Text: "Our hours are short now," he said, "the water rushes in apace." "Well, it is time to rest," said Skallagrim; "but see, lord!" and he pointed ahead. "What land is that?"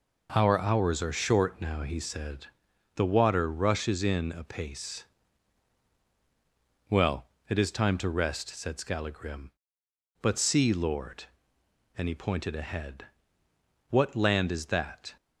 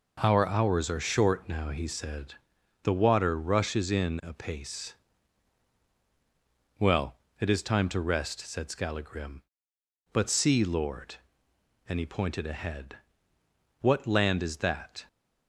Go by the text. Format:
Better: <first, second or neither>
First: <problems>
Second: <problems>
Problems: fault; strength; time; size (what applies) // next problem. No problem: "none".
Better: neither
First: none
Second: none